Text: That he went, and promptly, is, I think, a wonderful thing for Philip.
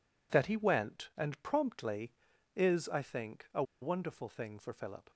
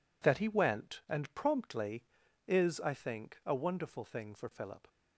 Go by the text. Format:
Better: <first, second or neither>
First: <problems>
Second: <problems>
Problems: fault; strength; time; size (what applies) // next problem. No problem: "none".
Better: second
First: pauses between "a" and "wonderful"; slight; at 3.6 s; 0.18 s long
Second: none